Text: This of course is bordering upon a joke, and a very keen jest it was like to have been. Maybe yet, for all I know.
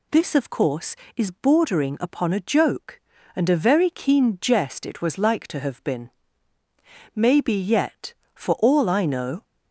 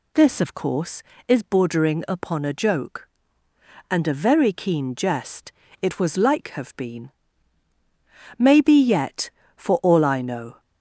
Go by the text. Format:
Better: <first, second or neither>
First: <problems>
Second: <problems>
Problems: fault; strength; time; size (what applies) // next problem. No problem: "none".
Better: first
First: none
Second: pauses between "jest" and "it"; slight; at 5.5 s; 0.30 s long // skips "to"; at 6.4 s